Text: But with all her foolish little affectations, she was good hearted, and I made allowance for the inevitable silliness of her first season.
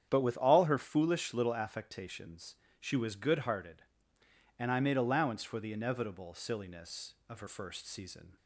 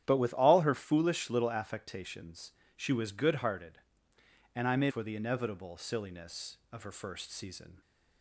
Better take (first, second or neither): first